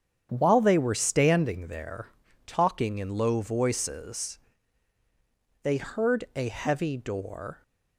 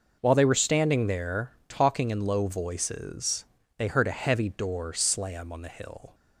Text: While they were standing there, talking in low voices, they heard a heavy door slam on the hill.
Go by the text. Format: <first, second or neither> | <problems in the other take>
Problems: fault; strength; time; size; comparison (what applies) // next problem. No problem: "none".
second | starts louder than the rest; strong; until 1.3 s; 8.5 dB // stops before "slam on the hill"; at 7.6 s